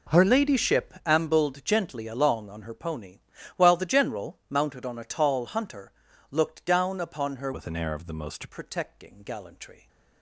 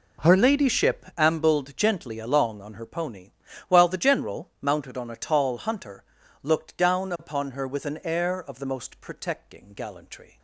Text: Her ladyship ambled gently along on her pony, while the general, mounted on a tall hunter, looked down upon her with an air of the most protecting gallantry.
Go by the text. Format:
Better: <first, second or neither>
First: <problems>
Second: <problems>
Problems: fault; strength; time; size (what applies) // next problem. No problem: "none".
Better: second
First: changes voice from "with" to "most"; from 7.5 to 8.5 s; 1.0 s long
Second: none